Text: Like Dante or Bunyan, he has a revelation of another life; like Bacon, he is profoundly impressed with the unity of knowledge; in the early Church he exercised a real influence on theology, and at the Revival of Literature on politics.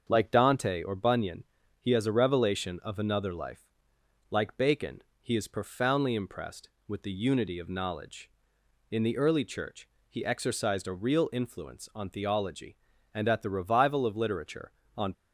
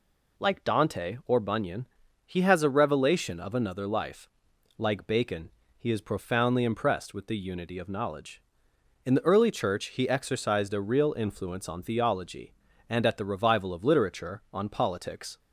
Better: second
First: starts louder than the rest; until 1.0 s; 7 dB // pauses between "Church" and "he"; slight; at 9.8 s; 0.20 s long // stops before "politics"; at 15.1 s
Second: none

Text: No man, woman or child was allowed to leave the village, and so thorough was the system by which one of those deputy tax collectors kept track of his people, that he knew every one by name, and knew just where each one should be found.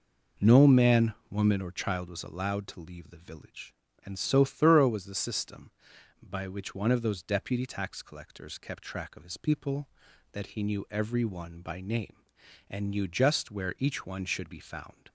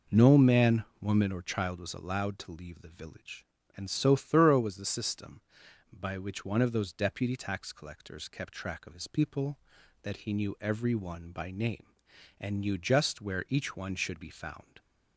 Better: neither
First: none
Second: none

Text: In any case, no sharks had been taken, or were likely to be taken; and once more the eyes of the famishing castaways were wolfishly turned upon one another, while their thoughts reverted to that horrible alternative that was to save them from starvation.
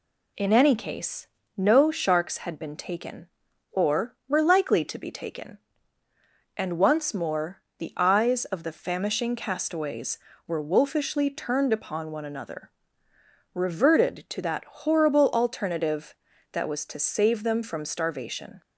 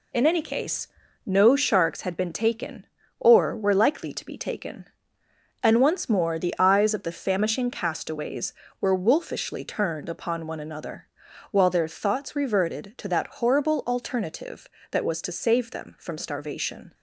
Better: second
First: pauses between "more" and "the"; slight; at 7.6 s; 0.18 s long // skips "while their thoughts"; at 13.1 s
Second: none

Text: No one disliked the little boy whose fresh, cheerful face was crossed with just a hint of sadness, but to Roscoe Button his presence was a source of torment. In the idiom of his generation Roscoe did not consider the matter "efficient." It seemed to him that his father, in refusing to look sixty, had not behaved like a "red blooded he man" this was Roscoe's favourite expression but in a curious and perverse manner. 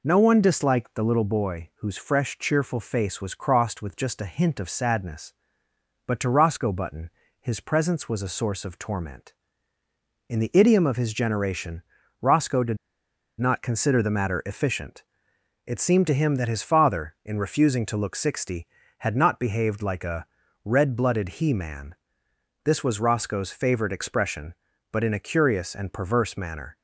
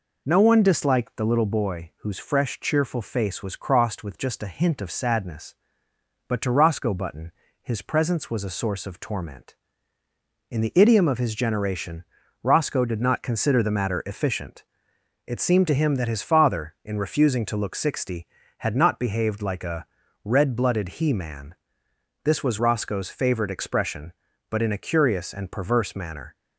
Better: second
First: pauses between "Button" and "his"; slight; at 7.0 s; 0.30 s long // pauses between "generation" and "Roscoe"; at 11.8 s; 0.40 s long // pauses between "did" and "not"; noticeable; at 12.7 s; 0.62 s long // pauses between "a" and "red"; at 20.2 s; 0.38 s long // pauses between "man" and "this"; noticeable; at 21.9 s; 0.70 s long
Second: pauses between "Button" and "his"; slight; at 7.3 s; 0.30 s long // pauses between "generation" and "Roscoe"; at 12.0 s; 0.40 s long // pauses between "a" and "red"; at 19.8 s; 0.38 s long // pauses between "man" and "this"; noticeable; at 21.5 s; 0.70 s long

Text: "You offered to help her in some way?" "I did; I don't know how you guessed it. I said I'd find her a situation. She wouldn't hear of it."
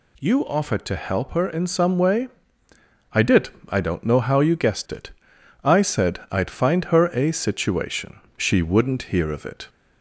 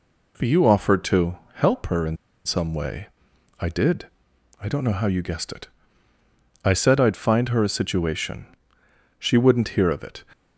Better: first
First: none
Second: pauses between "to" and "help"; slight; at 1.3 s; 0.16 s long // pauses between "in" and "some"; slight; at 2.1 s; 0.30 s long

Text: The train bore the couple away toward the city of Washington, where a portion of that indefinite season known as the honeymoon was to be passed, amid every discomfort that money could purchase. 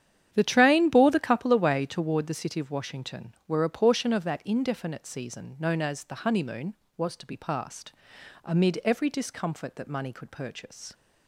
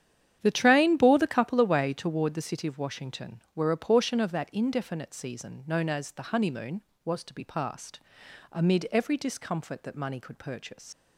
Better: first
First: starts louder than the rest; strong; until 1.3 s; 9.5 dB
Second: starts louder than the rest; strong; until 1.4 s; 9.5 dB // leaves "purchase" unfinished; at 10.9 s; 80 ms

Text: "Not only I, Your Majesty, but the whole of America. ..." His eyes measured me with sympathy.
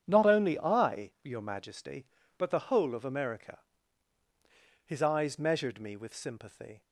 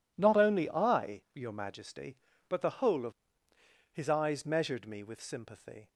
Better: first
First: starts louder than the rest; strong; until 1.0 s; 10 dB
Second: starts louder than the rest; strong; until 1.1 s; 9 dB // skips "America"; at 3.1 s

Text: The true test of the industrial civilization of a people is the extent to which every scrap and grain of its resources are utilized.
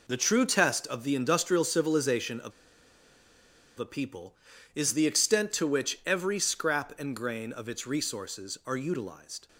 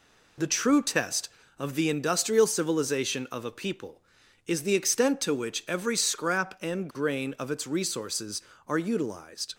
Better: second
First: pauses between "of" and "a"; strong; at 2.5 s; 1.2 s long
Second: none

